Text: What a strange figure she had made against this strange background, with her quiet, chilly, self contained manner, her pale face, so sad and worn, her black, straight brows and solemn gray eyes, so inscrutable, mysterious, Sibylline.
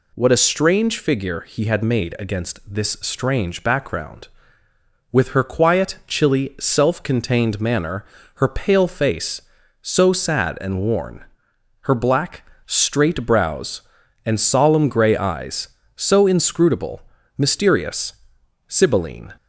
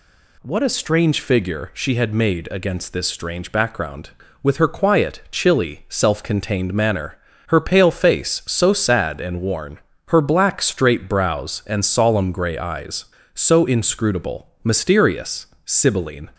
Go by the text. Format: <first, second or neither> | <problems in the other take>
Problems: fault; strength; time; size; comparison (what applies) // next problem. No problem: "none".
second | says "he" for "she"; at 1.3 s